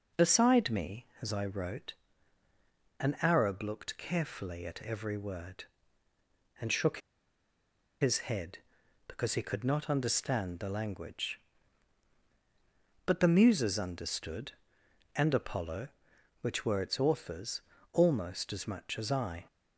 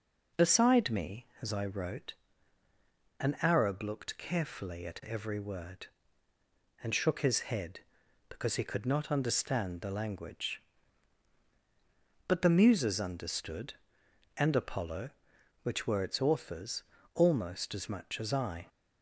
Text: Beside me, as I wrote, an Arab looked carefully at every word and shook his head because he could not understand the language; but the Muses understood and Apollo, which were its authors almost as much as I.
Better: second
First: pauses between "shook" and "his"; at 6.9 s; 1.0 s long // pauses between "authors" and "almost"; slight; at 17.6 s; 0.30 s long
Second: pauses between "authors" and "almost"; slight; at 16.8 s; 0.30 s long

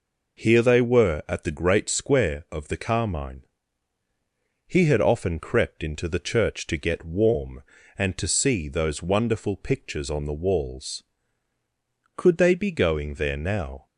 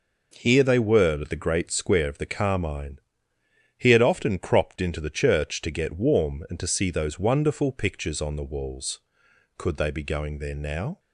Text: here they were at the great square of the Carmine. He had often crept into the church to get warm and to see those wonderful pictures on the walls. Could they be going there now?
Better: first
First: none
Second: says "cropped" for "crept"; at 4.3 s

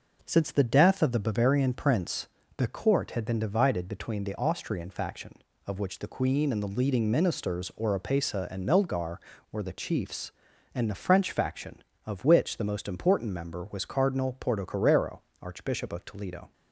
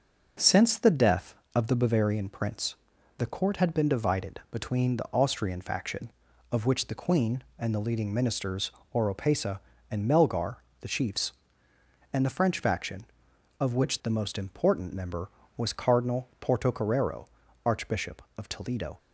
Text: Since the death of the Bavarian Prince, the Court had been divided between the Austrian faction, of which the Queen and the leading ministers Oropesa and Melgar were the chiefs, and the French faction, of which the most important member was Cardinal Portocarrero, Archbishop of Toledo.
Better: first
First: none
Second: pauses between "ministers" and "Oropesa"; slight; at 8.7 s; 0.24 s long // skips "were"; at 10.6 s

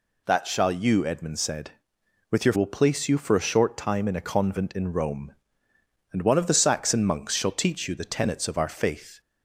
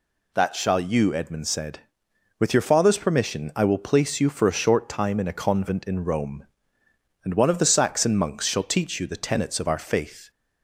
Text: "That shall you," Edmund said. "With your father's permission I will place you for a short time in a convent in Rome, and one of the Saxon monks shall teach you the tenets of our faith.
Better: second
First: skips "father's permission I"; at 2.5 s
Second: none

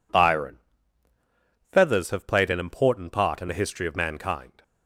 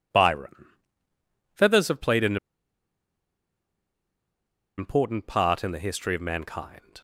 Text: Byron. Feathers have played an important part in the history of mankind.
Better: first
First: none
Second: pauses between "an" and "important"; strong; at 2.3 s; 2.4 s long

